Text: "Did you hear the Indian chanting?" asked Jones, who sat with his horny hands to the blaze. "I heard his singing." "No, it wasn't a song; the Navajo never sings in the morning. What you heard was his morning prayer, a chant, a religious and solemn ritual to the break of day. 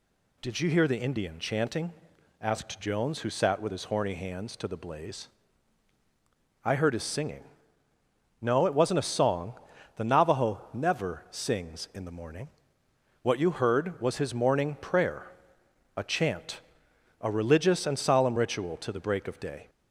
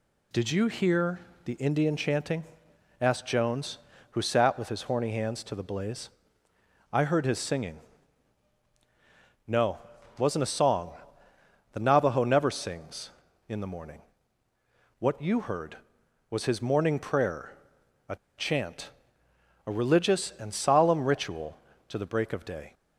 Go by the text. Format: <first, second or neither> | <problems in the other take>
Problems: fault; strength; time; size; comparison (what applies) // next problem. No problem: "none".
first | pauses between "hear" and "the"; slight; at 1.1 s; 0.24 s long // pauses between "a" and "chant"; slight; at 18.1 s; 0.21 s long